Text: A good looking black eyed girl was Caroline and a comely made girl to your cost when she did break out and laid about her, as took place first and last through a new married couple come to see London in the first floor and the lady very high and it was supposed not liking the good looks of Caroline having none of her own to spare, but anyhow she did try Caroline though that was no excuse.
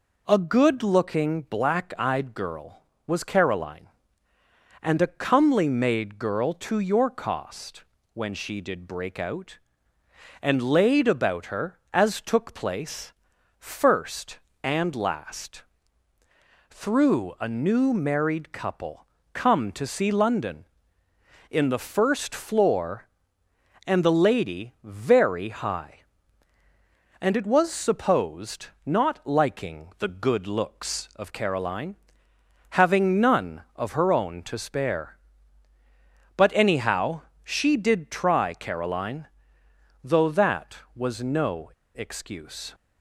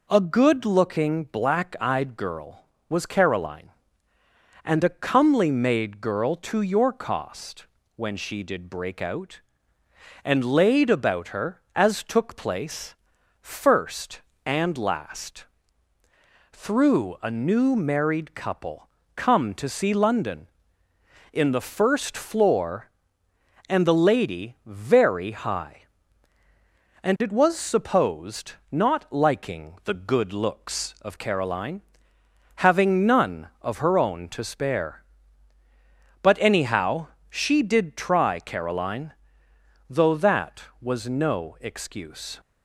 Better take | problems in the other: second | pauses between "cost" and "when"; slight; at 7.8 s; 0.32 s long; slight in the second // pauses between "place" and "first"; noticeable; at 13.1 s; 0.46 s long; noticeable in the second // pauses between "last" and "through"; at 15.6 s; 1.1 s long; also in the second // pauses between "couple" and "come"; slight; at 19.0 s; 0.28 s long; slight in the second // pauses between "supposed" and "not"; slight; at 28.6 s; 0.18 s long; slight in the second // pauses between "Caroline" and "having"; noticeable; at 31.9 s; 0.76 s long; noticeable in the second // pauses between "anyhow" and "she"; slight; at 37.2 s; 0.24 s long; slight in the second // pauses between "Caroline" and "though"; noticeable; at 39.2 s; 0.76 s long; noticeable in the second // pauses between "no" and "excuse"; slight; at 41.7 s; 0.23 s long

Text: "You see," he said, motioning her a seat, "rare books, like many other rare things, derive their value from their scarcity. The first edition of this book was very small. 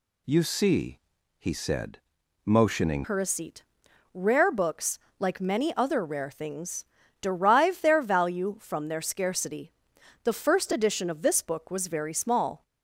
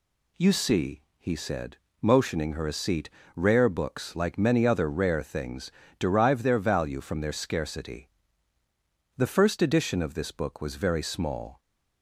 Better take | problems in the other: second | changes voice at "her"; from 3.0 s on; 9.6 s long

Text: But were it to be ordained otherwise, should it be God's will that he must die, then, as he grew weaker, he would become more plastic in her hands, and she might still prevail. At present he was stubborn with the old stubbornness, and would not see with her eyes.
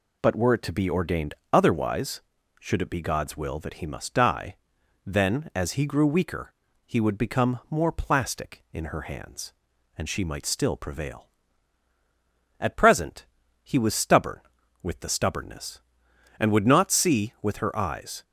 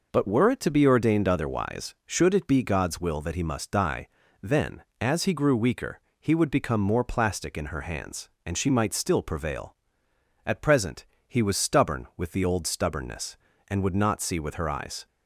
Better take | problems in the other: second | pauses between "ordained" and "otherwise"; slight; at 1.3 s; 0.20 s long // pauses between "present" and "he"; at 13.2 s; 0.38 s long; slight in the second // skips "old"; at 15.0 s

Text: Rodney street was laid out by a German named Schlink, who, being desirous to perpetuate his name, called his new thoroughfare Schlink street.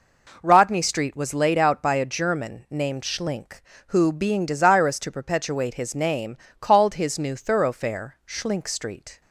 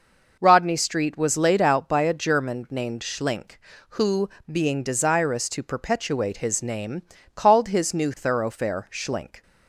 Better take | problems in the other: first | stops before "street"; at 9.4 s

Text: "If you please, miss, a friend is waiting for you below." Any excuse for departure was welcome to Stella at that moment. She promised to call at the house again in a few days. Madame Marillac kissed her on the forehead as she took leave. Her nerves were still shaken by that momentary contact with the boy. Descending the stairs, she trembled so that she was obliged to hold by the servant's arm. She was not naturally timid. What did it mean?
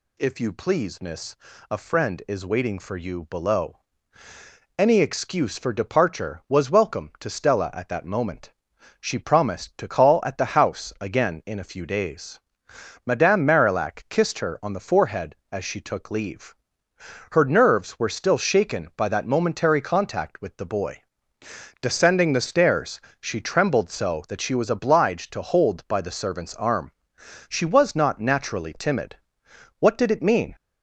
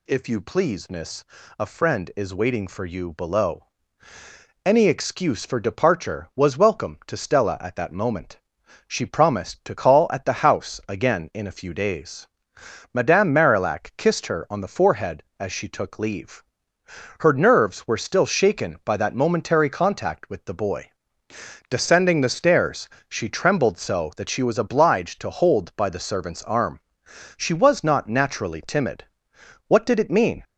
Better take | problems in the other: neither | none

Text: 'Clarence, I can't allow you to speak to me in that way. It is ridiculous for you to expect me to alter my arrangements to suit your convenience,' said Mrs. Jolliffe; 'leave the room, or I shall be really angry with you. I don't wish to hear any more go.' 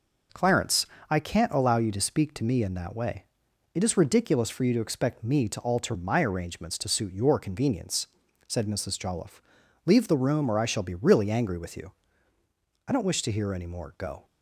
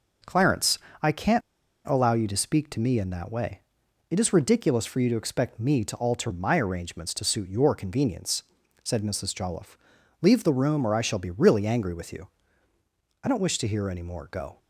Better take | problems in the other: first | pauses between "can't" and "allow"; at 1.4 s; 0.45 s long

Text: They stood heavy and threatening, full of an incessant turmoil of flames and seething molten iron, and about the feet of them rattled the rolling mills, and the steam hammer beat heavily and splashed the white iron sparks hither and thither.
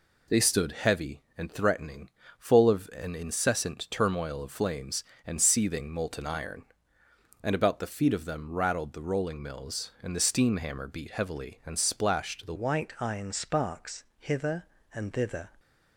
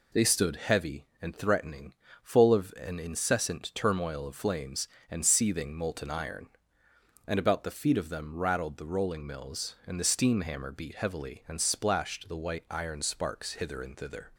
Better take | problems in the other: second | changes voice at "white"; from 12.5 s on; 3.0 s long // pauses between "sparks" and "hither"; slight; at 14.0 s; 0.16 s long

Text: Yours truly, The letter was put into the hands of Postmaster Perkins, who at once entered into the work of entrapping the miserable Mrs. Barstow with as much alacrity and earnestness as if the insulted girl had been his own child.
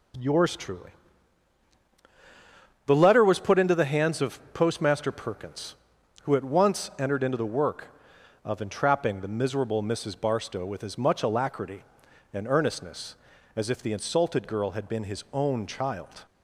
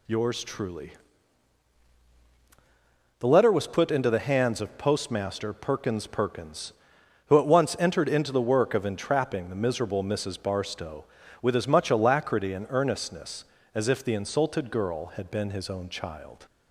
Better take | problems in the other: first | says "Perkins" twice; at 6.0 s

